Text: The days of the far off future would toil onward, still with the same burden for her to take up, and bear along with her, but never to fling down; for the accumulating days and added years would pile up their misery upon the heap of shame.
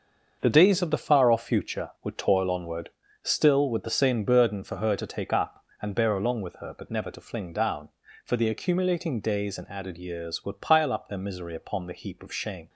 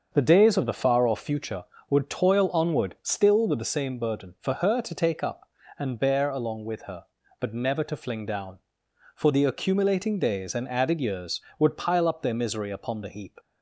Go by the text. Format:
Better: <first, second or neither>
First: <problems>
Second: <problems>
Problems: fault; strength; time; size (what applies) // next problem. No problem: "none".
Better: first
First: starts louder than the rest; until 1.4 s; 6.5 dB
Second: starts louder than the rest; until 1.1 s; 6.5 dB // stops before "of shame"; at 13.3 s